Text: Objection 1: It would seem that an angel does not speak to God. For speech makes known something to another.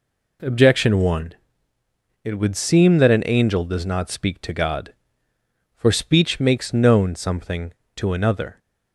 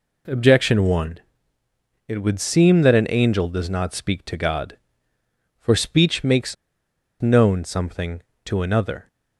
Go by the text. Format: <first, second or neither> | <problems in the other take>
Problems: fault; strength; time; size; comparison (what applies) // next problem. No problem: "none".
first | pauses between "makes" and "known"; noticeable; at 6.5 s; 0.66 s long